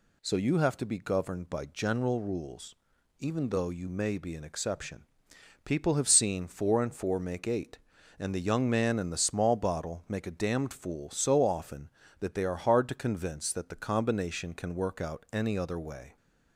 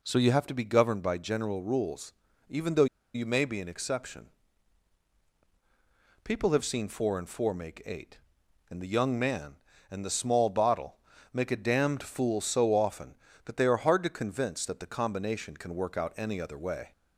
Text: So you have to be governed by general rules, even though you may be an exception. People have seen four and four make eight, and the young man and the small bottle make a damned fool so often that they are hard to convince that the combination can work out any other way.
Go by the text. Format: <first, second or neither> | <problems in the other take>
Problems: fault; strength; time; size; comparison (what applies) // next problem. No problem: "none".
first | pauses between "though" and "you"; slight; at 2.8 s; 0.28 s long // pauses between "bottle" and "make"; slight; at 10.9 s; 0.36 s long